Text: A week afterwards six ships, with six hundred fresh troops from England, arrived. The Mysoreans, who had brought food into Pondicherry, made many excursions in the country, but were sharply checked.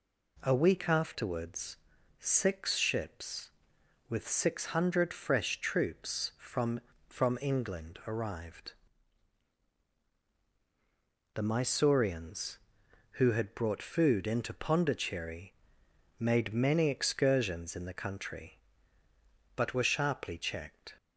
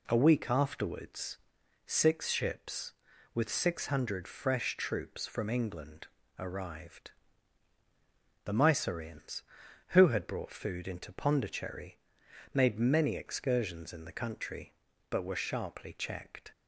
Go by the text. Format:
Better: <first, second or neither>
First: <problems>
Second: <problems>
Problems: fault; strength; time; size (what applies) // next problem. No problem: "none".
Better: second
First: pauses between "afterwards" and "six"; at 1.7 s; 0.42 s long // says "from" twice; at 7.0 s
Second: pauses between "afterwards" and "six"; noticeable; at 1.3 s; 0.48 s long